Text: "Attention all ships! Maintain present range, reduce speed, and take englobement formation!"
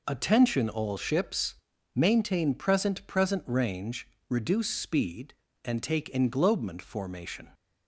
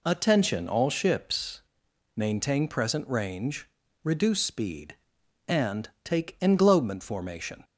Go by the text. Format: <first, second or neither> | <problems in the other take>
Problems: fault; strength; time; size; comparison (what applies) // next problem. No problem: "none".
second | says "present" twice; at 3.0 s